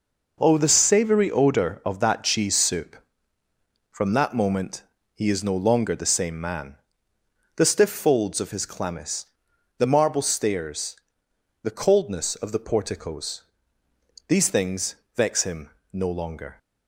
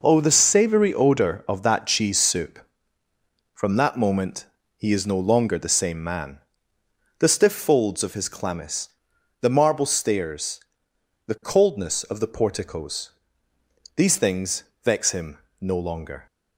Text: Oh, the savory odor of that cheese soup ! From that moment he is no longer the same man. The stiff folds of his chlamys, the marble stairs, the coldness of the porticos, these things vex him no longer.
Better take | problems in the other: neither | pauses between "moment" and "he"; slight; the same in both // pauses between "things" and "vex"; slight; the same in both // pauses between "him" and "no"; slight; the same in both

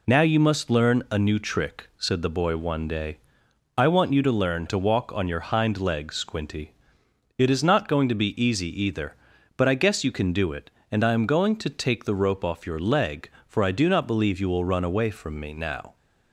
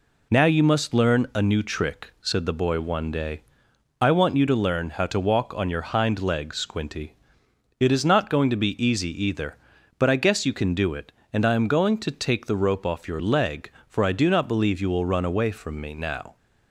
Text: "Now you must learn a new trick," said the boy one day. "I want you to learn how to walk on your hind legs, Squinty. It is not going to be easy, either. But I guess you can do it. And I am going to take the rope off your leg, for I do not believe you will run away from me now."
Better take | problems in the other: second | skips "how"; at 4.6 s

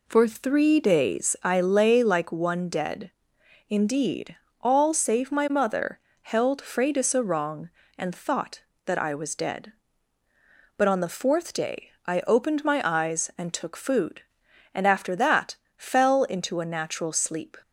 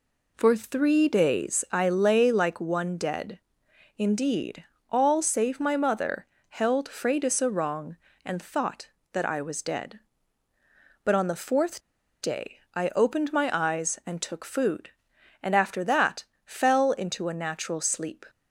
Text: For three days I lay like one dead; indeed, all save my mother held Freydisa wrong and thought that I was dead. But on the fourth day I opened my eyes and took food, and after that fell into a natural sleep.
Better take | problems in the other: first | pauses between "mother" and "held"; slight; at 6.2 s; 0.22 s long; slight in the first // pauses between "fourth" and "day"; at 11.7 s; 0.43 s long // pauses between "that" and "fell"; slight; at 16.2 s; 0.18 s long; slight in the first

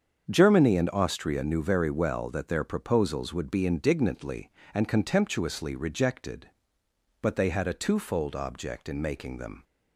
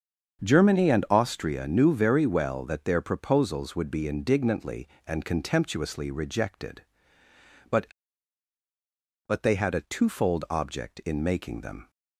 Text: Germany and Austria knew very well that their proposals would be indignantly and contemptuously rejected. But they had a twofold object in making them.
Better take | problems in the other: first | starts louder than the rest; until 1.5 s; 7 dB; strong in the first // says "But" twice; at 9.2 s

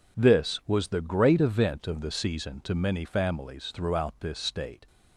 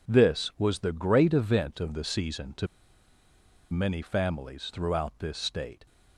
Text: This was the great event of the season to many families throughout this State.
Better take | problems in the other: first | pauses between "to" and "many"; at 2.6 s; 1.0 s long

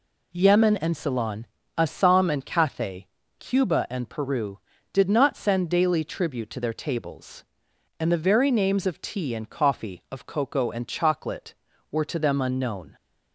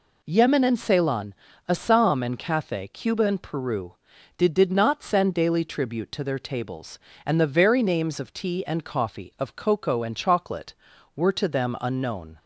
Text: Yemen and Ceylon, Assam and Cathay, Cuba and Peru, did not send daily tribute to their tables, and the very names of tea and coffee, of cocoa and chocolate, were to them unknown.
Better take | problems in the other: first | says "did" twice; at 4.5 s

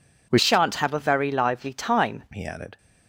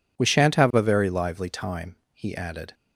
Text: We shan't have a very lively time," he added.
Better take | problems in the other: second | changes voice from "shan't" to "time"; from 0.3 to 2.2 s; 1.9 s long

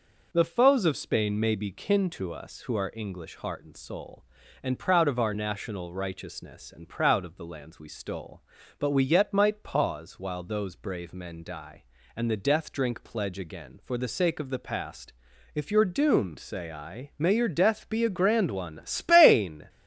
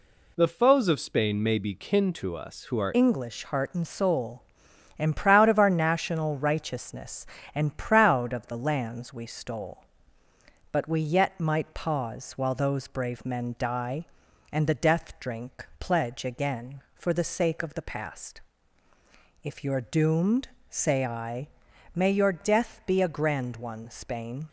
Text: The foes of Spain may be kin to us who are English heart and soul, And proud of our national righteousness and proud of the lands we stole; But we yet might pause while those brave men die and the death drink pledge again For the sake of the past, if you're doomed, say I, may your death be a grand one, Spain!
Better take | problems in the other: first | changes voice at "English"; from 2.9 s on; 21.5 s long

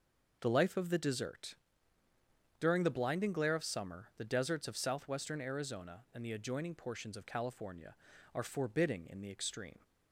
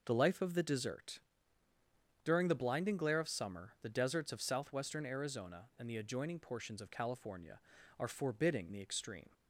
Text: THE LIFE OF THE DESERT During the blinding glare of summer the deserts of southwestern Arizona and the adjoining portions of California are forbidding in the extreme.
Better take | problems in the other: first | pauses between "DESERT" and "During"; at 1.1 s; 1.0 s long; also in the first // skips "in"; at 8.7 s

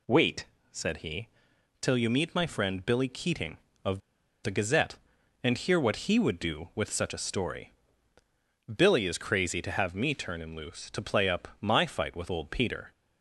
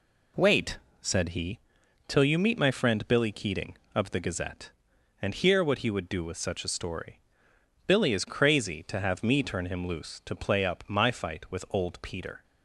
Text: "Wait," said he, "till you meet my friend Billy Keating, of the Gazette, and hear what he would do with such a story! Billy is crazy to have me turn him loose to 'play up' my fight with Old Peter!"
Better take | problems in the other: second | pauses between "of" and "the"; at 4.0 s; 0.43 s long

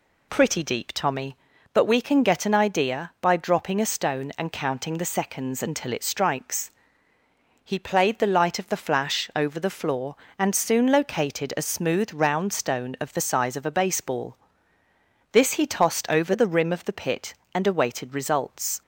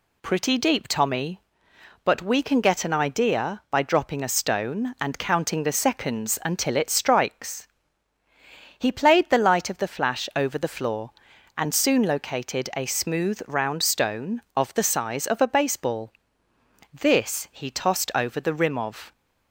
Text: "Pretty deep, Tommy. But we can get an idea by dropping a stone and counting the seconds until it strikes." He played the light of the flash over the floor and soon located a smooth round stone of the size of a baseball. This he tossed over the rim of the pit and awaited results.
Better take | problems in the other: first | stops before "the pit and awaited results"; at 19.1 s

